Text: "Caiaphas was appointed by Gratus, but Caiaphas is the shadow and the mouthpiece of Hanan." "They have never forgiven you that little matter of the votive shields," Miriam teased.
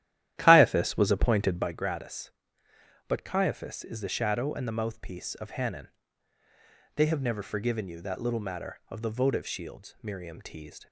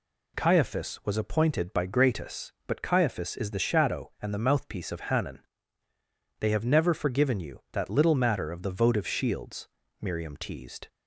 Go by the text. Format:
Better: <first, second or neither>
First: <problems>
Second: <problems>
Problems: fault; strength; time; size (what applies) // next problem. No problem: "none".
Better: second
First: starts louder than the rest; strong; until 1.8 s; 12.5 dB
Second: none